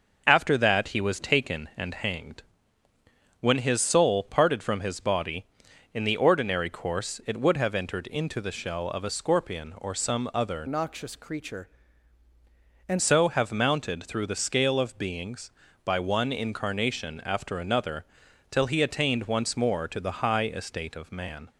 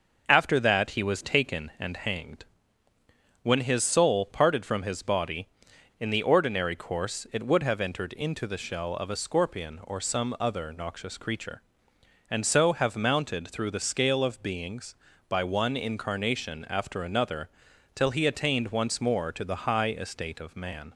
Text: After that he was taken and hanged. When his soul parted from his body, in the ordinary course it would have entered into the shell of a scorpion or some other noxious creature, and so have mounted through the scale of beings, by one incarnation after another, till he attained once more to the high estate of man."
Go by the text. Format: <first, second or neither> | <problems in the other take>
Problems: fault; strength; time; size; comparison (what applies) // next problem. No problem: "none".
second | changes voice from "noxious" to "and"; from 10.6 to 13.0 s; 2.4 s long